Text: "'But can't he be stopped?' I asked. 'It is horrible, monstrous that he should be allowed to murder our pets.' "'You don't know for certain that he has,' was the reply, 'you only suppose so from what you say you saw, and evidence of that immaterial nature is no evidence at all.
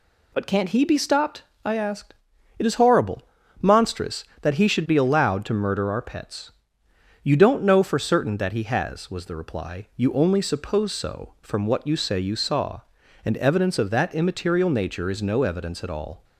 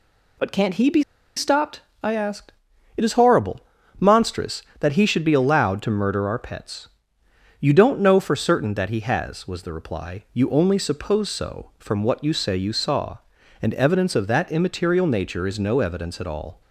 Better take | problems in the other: first | pauses between "be" and "stopped"; slight; at 1.0 s; 0.34 s long

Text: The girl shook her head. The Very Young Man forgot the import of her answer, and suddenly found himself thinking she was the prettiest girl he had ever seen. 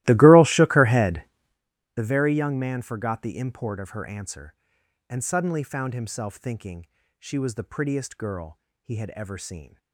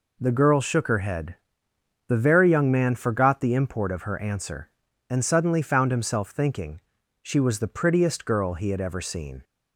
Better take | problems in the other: second | starts louder than the rest; strong; until 1.6 s; 17 dB // pauses between "thinking" and "she"; slight; at 6.8 s; 0.32 s long; also in the second // pauses between "girl" and "he"; slight; at 8.5 s; 0.24 s long

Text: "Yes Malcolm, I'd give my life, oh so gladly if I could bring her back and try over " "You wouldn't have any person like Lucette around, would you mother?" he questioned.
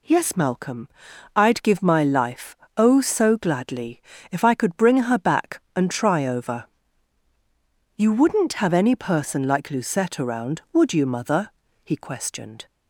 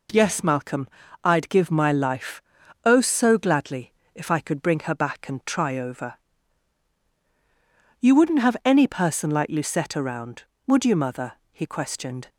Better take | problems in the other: neither | pauses between "gladly" and "if"; slight; the same in both

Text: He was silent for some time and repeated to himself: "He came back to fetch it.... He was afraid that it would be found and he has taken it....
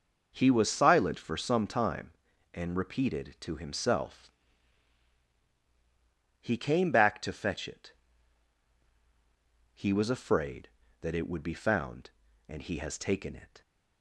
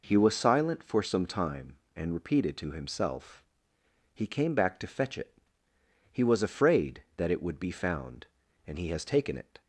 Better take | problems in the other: neither | none

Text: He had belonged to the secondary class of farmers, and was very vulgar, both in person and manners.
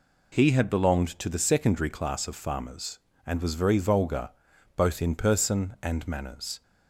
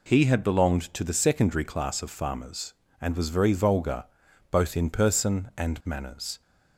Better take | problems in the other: neither | none

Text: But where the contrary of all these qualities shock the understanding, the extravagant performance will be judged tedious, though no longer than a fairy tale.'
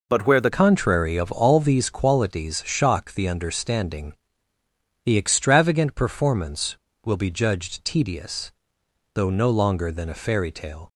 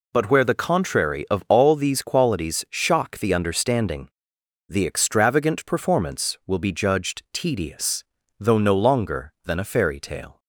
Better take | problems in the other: second | changes voice at "contrary"; from 0.5 s on; 10.3 s long

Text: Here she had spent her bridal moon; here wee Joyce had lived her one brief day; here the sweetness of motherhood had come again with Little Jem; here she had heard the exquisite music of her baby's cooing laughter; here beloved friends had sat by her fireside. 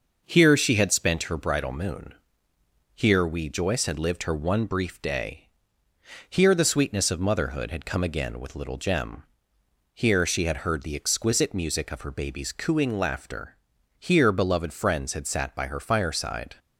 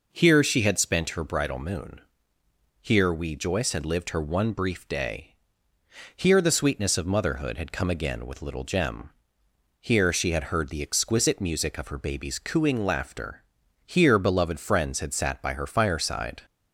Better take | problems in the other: second | gets quieter; slight; throughout; 3.5 dB

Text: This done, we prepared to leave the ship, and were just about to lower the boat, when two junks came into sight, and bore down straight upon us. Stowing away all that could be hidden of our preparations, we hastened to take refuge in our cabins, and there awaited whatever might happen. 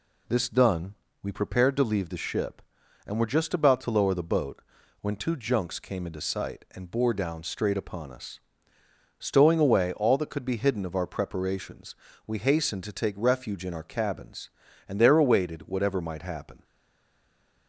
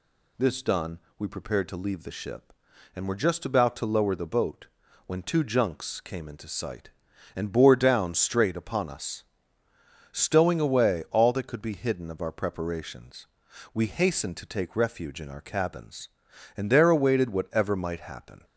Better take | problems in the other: second | stays silent after the last word; from 16.6 s on; 1.0 s long

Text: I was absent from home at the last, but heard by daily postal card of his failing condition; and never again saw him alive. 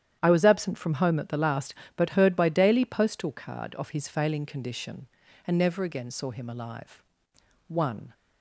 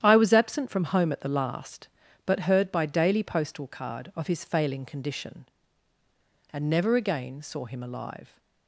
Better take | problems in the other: second | starts louder than the rest; strong; until 1.2 s; 10 dB; strong in the second // goes on to say "One"; slight; from 7.6 s on; 0.46 s long

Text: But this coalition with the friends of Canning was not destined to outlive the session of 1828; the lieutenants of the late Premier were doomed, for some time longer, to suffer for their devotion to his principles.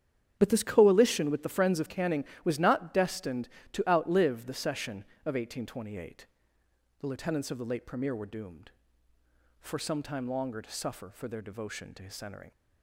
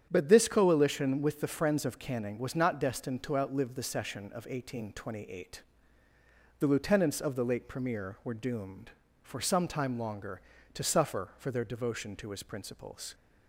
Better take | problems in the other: second | starts louder than the rest; strong; until 1.3 s; 8.5 dB; strong in the second // says "centering" for "principles"; at 12.1 s

